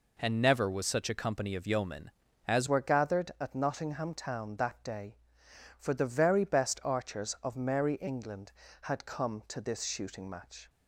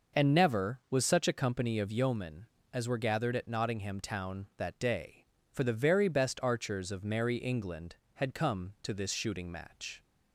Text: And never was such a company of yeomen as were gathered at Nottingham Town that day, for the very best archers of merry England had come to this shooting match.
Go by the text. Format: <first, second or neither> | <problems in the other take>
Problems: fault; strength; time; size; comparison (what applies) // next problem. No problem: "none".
second | changes voice at "were"; from 2.6 s on; 8.0 s long